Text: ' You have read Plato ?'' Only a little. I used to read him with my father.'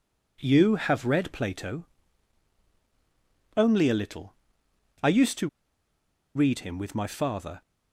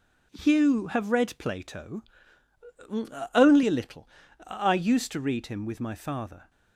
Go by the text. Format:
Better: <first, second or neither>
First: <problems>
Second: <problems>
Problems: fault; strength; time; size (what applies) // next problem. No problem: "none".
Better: second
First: pauses between "to" and "read"; noticeable; at 5.4 s; 0.86 s long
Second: none